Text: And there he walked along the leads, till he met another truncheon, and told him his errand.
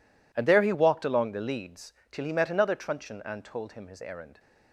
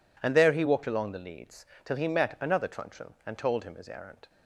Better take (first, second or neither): neither